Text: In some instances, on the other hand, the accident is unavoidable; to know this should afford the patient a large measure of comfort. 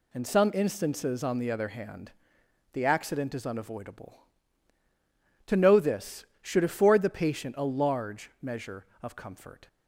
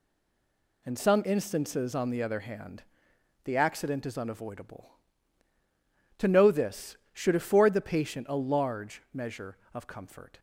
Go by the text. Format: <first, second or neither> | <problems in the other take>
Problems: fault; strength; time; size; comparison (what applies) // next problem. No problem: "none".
first | stays silent before the first word; slight; until 0.8 s; 0.8 s long